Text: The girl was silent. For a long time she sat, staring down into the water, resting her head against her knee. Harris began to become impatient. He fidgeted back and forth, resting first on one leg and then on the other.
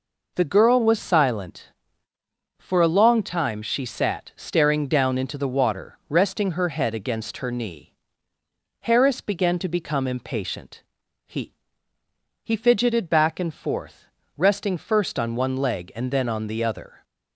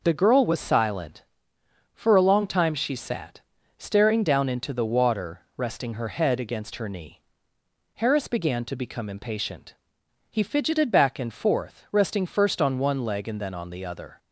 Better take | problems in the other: second | says "He" twice; at 12.4 s

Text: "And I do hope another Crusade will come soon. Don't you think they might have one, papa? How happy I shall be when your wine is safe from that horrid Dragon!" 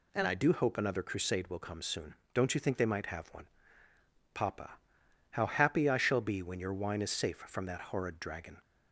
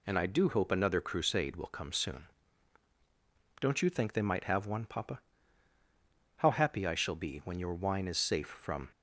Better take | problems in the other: first | stops before "that horrid Dragon"; at 8.9 s

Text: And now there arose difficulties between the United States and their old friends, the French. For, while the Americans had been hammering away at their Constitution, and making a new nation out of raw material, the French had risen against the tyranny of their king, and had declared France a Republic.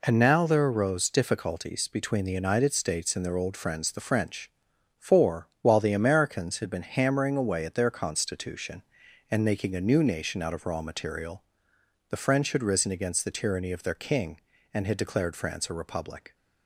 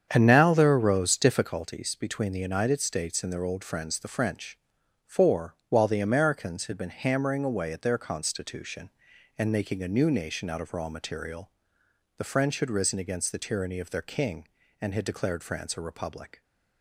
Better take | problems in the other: first | starts louder than the rest; strong; until 1.5 s; 7.5 dB

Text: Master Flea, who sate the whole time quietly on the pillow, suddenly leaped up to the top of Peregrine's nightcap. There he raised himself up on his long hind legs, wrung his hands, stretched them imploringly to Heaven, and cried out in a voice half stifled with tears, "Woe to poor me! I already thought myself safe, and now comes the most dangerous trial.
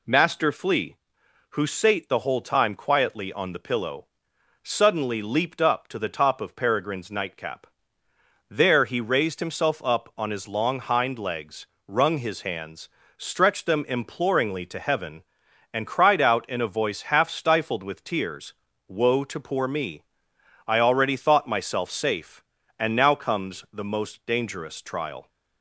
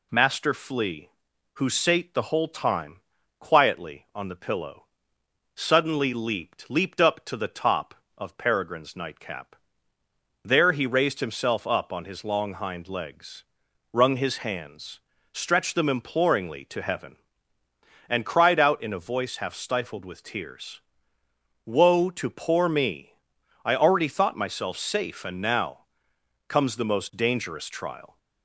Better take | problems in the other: first | pauses between "time" and "quietly"; at 3.0 s; 0.38 s long // says "leaped" twice; at 6.7 s // pauses between "now" and "comes"; noticeable; at 25.8 s; 0.62 s long

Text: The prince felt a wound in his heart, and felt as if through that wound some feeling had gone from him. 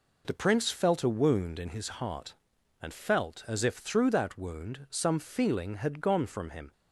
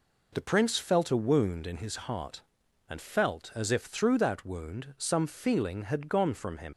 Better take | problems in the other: first | leaves "him" unfinished; at 6.7 s; 65 ms

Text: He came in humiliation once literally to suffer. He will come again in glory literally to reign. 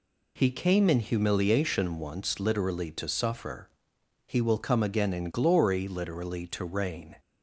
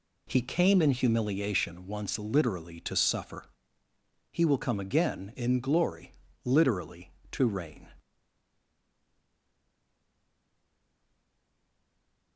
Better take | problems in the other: first | pauses between "glory" and "literally"; slight; at 6.1 s; 0.32 s long // stays silent after the last word; strong; from 8.0 s on; 4.3 s long

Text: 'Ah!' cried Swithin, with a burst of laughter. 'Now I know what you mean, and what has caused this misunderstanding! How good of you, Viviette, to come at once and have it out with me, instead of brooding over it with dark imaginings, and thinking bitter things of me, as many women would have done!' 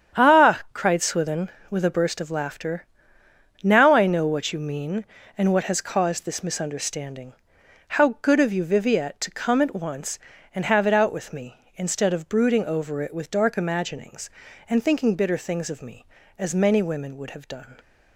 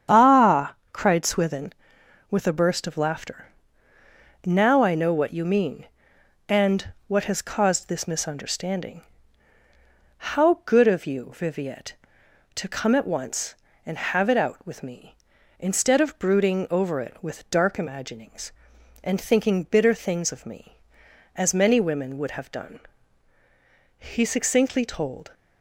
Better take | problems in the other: first | starts louder than the rest; strong; until 1.3 s; 8.5 dB; strong in the first // pauses between "and" and "what"; slight; at 6.9 s; 0.16 s long // goes on to say "He succinctly told"; from 23.9 s on; 1.3 s long

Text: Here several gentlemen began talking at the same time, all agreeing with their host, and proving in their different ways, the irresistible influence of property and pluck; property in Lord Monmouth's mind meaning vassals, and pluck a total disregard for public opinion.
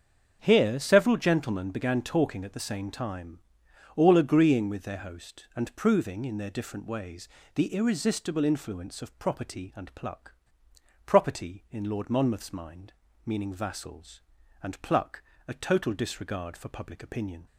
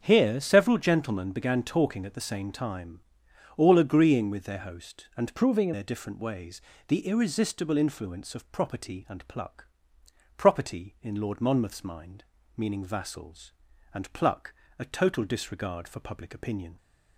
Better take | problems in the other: first | starts louder than the rest; until 1.0 s; 7 dB; also in the first // changes voice from "proving" to "in"; from 5.3 to 5.7 s; 0.4 s long // pauses between "mind" and "meaning"; slight; at 12.2 s; 0.32 s long; slight in the first // pauses between "pluck" and "a"; slight; at 14.5 s; 0.24 s long; slight in the first

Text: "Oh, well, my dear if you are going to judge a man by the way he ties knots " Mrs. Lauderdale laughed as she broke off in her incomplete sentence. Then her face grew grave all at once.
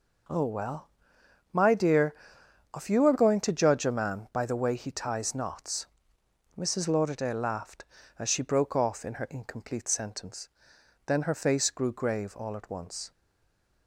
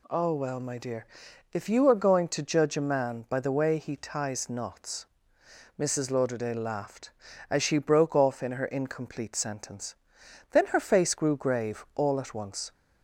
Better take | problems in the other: second | pauses between "dear" and "if"; noticeable; at 2.1 s; 0.60 s long; noticeable in the second // stays silent after the last word; slight; from 13.1 s on; 0.7 s long

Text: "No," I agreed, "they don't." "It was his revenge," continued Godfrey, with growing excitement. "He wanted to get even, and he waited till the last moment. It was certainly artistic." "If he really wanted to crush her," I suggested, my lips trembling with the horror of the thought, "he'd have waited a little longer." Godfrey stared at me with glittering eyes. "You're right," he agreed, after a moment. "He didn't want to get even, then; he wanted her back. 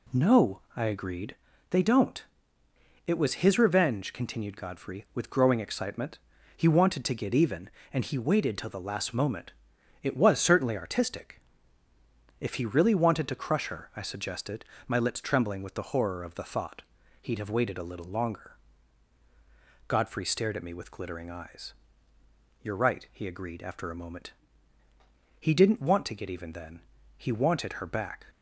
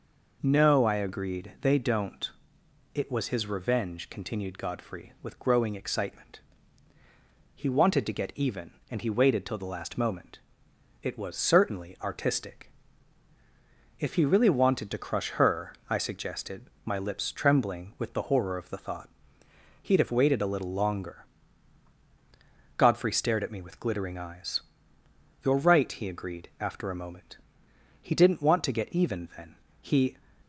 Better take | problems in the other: first | stops before "wanted her back"; at 30.4 s

